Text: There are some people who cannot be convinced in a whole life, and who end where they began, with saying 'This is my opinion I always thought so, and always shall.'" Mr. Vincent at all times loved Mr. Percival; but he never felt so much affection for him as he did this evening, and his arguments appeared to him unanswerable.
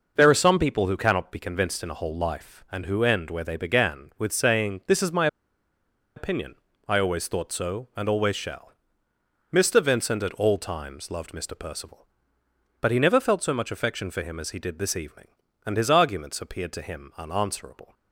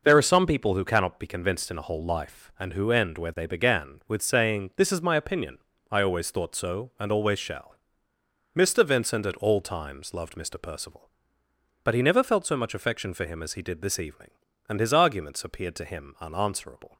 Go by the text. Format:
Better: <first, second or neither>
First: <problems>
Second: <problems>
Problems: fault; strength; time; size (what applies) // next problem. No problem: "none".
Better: second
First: pauses between "my" and "opinion"; noticeable; at 5.2 s; 0.89 s long // pauses between "opinion" and "I"; slight; at 6.5 s; 0.32 s long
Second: pauses between "opinion" and "I"; slight; at 5.5 s; 0.32 s long